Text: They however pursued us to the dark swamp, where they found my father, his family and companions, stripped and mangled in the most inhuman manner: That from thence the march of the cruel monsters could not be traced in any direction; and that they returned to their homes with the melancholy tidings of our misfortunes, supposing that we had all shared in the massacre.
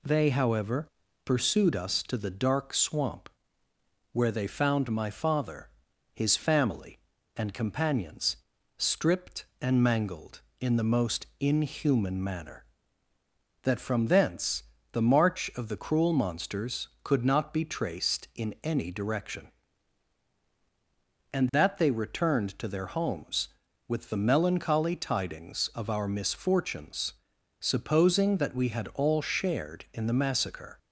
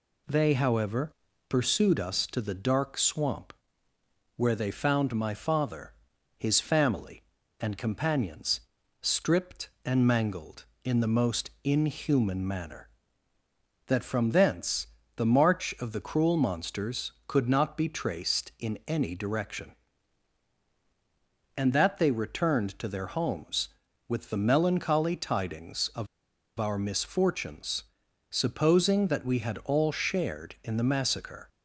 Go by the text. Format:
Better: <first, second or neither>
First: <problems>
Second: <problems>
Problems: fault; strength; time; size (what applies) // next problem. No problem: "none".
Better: first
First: pauses between "however" and "pursued"; slight; at 0.8 s; 0.36 s long // pauses between "thence" and "the"; slight; at 14.6 s; 0.30 s long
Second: pauses between "however" and "pursued"; slight; at 1.1 s; 0.36 s long // pauses between "thence" and "the"; slight; at 14.8 s; 0.30 s long // pauses between "of" and "our"; noticeable; at 26.0 s; 0.53 s long